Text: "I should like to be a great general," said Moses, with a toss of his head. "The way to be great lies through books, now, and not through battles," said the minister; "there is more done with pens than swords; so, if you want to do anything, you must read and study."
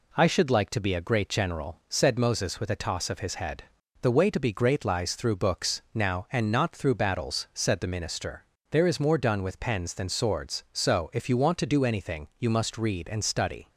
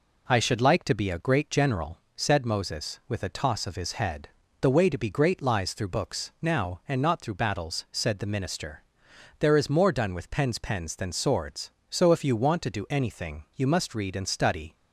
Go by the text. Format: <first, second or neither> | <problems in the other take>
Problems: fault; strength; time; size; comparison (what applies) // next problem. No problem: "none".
first | says "pens" twice; at 10.5 s